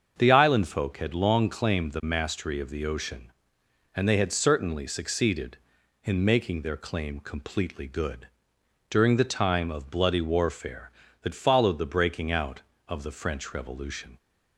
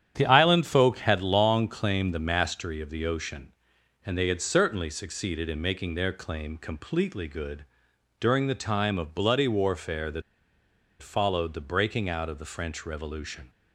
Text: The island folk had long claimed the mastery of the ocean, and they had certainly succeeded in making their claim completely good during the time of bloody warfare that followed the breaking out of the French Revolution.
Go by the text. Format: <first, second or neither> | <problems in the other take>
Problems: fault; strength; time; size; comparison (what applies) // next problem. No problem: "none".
first | starts louder than the rest; strong; until 1.1 s; 10 dB; also in the first // pauses between "good" and "during"; noticeable; at 7.6 s; 0.52 s long; noticeable in the first // pauses between "that" and "followed"; noticeable; at 10.2 s; 0.79 s long